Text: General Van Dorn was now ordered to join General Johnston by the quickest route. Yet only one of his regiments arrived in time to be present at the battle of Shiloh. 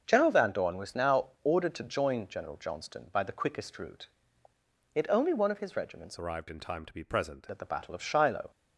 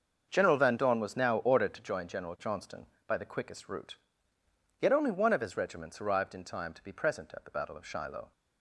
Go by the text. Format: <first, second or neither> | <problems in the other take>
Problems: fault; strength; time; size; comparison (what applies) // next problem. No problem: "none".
second | starts louder than the rest; until 1.0 s; 6.5 dB; also in the second // changes voice from "arrived" to "present"; from 6.1 to 7.4 s; 1.3 s long